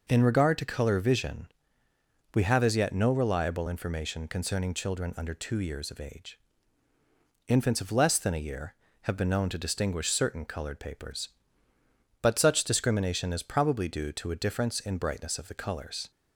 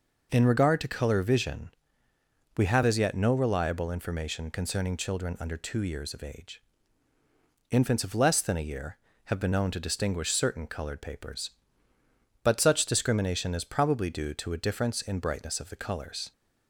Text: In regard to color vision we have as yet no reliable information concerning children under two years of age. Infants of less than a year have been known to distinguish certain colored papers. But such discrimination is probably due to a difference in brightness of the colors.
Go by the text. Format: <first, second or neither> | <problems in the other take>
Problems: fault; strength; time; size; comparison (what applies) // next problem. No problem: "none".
neither | pauses between "vision" and "we"; noticeable; the same in both